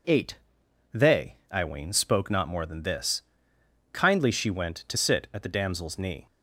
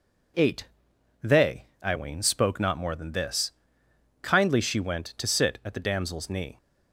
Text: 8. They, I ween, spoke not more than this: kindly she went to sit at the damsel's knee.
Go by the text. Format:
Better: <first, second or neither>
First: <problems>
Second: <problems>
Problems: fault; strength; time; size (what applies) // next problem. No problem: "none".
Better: neither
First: none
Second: none